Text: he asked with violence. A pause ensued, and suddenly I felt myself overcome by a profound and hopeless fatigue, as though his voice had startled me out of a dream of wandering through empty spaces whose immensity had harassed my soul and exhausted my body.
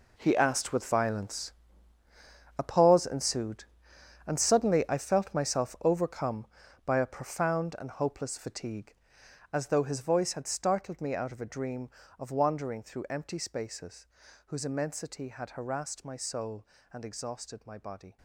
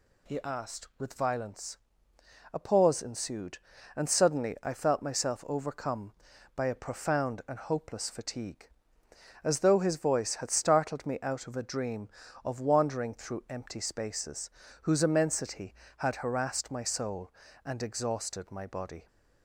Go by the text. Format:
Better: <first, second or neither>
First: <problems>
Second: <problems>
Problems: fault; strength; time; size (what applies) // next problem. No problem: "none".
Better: second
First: gets quieter; strong; throughout; 13.5 dB // pauses between "spaces" and "whose"; at 14.0 s; 0.40 s long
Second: pauses between "spaces" and "whose"; slight; at 14.5 s; 0.32 s long